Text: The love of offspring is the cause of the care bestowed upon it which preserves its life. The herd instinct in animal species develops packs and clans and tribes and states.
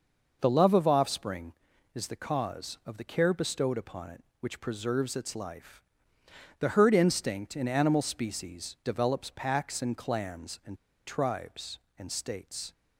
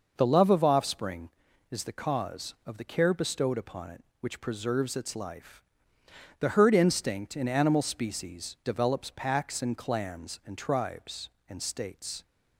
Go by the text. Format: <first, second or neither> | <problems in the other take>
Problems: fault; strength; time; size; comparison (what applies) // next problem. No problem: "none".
second | pauses between "and" and "tribes"; slight; at 10.7 s; 0.30 s long